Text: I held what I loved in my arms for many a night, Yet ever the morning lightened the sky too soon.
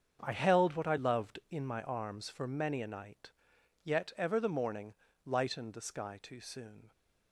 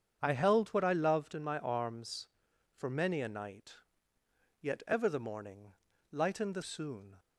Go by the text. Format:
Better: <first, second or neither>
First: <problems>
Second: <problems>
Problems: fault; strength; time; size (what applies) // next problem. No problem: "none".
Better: first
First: starts louder than the rest; until 1.2 s; 7 dB // pauses between "morning" and "lightened"; slight; at 4.9 s; 0.30 s long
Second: starts louder than the rest; strong; until 1.2 s; 7.5 dB // pauses between "morning" and "lightened"; slight; at 5.7 s; 0.36 s long // skips "sky too"; at 6.6 s